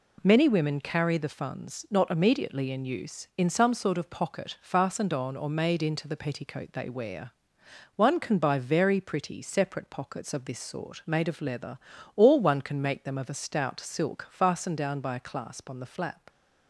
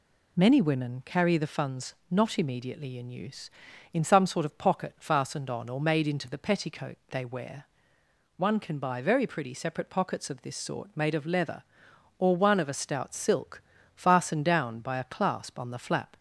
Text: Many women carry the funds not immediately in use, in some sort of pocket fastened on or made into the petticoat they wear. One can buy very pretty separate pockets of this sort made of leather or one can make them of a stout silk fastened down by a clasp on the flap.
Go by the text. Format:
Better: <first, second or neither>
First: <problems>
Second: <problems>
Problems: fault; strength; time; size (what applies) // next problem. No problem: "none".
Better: first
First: none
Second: pauses between "funds" and "not"; slight; at 1.9 s; 0.18 s long // skips "can make them"; at 12.5 s // pauses between "silk" and "fastened"; slight; at 13.6 s; 0.32 s long